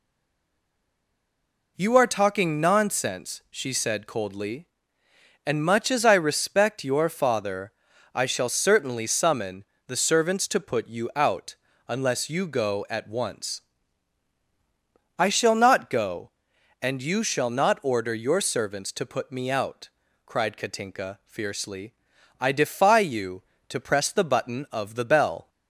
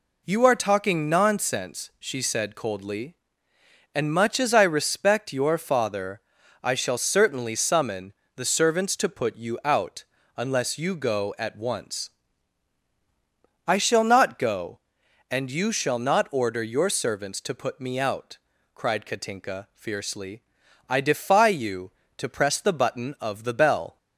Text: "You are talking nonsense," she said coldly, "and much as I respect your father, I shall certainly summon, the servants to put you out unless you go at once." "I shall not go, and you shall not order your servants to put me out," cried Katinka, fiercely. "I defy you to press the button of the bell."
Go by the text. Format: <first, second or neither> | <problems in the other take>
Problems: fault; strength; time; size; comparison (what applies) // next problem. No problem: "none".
second | stays silent before the first word; noticeable; until 1.7 s; 1.7 s long // pauses between "out" and "unless"; slight; at 11.5 s; 0.32 s long; slight in the second